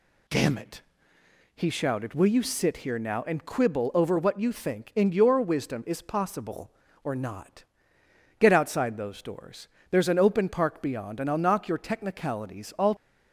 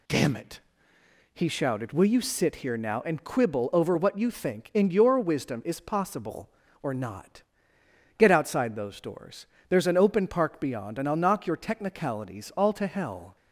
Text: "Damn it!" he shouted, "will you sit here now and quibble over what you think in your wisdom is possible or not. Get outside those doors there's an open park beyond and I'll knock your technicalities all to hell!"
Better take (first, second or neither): second